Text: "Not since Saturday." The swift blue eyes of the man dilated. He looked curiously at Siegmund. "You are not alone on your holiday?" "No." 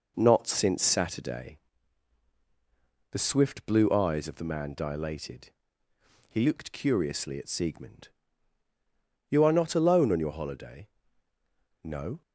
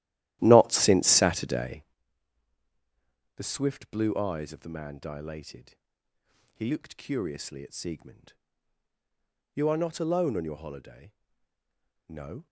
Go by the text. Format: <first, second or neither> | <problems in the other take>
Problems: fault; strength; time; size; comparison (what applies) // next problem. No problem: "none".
first | starts louder than the rest; strong; until 2.0 s; 14 dB